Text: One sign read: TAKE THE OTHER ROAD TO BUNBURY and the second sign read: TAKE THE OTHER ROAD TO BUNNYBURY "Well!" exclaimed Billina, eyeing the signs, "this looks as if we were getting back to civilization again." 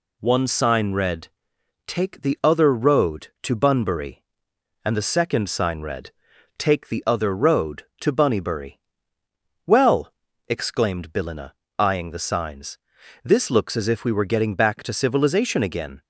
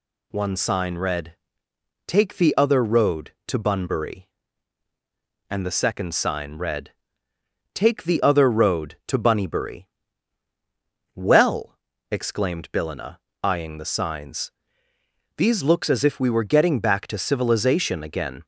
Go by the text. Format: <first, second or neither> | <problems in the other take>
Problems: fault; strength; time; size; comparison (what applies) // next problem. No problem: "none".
first | pauses between "BUNNYBURY" and "Well"; strong; at 9.8 s; 1.2 s long; noticeable in the first // says "these" for "this"; at 15.3 s